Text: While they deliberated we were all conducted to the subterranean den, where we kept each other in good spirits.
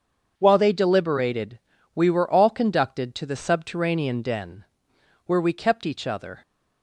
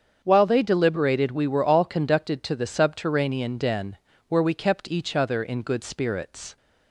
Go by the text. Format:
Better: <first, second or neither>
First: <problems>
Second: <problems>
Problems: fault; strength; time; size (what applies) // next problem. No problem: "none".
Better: second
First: starts louder than the rest; until 1.3 s; 7 dB // pauses between "deliberated" and "we"; slight; at 1.5 s; 0.36 s long // stops before "in good spirits"; at 6.4 s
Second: starts louder than the rest; strong; until 1.2 s; 7.5 dB